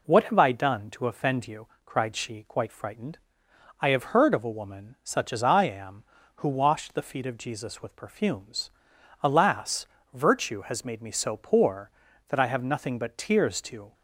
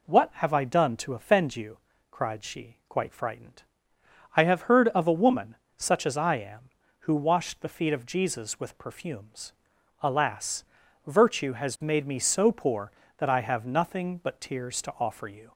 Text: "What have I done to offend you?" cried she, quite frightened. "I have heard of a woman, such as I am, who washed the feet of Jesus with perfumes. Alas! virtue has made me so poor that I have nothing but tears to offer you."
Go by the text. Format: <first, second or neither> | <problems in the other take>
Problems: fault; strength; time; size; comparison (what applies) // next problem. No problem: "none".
second | stops before "offer you"; at 13.9 s